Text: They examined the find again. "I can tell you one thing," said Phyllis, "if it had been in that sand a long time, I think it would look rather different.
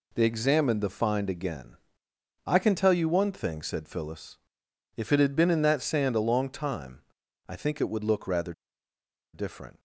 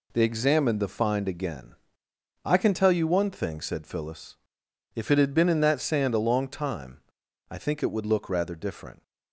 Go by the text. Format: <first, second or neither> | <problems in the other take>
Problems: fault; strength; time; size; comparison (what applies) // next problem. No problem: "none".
second | pauses between "rather" and "different"; noticeable; at 8.5 s; 0.81 s long